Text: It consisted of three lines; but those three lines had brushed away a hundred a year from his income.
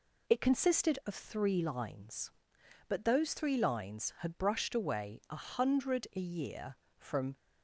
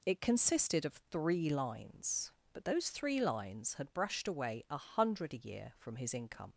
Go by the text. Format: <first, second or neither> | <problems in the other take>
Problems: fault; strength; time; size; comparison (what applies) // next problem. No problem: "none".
second | stops before "his income"; at 7.3 s